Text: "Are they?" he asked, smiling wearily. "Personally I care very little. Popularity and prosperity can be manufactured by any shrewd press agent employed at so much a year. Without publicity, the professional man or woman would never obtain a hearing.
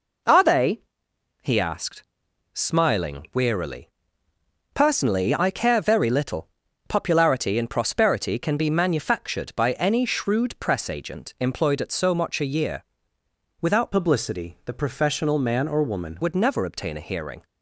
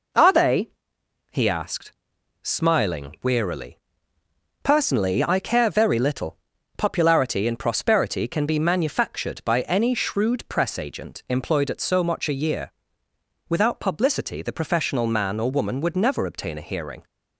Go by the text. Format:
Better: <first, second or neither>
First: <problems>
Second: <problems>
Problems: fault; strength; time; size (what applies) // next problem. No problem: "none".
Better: second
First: changes voice from "publicity" to "woman"; from 13.9 to 16.1 s; 2.2 s long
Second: none